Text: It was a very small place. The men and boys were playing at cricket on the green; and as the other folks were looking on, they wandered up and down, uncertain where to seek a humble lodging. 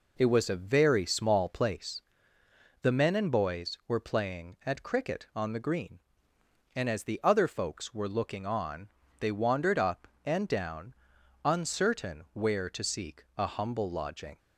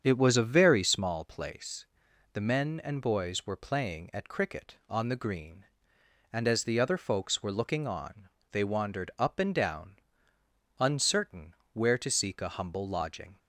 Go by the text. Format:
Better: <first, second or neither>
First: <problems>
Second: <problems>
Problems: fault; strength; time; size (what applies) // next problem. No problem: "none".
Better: first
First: none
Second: starts louder than the rest; strong; until 1.3 s; 7.5 dB // pauses between "uncertain" and "where"; slight; at 11.5 s; 0.20 s long